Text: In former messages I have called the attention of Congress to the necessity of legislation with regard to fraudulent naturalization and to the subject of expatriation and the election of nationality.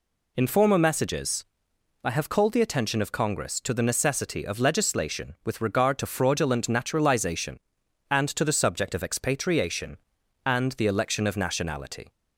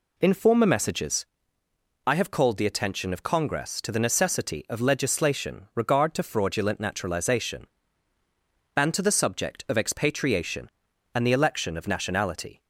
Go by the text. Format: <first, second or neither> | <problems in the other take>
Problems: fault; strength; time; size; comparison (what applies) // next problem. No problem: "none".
first | pauses between "messages" and "I"; noticeable; at 1.2 s; 0.80 s long; noticeable in the first // skips "with"; at 5.7 s